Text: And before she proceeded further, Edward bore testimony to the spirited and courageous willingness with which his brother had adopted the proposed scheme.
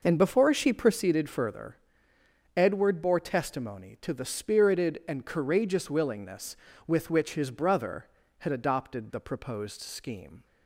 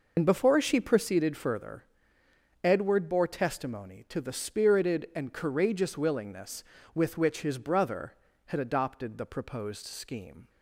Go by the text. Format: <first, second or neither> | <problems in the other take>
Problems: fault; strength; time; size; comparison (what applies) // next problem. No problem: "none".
first | loses the start of "And"; at 0.1 s; 65 ms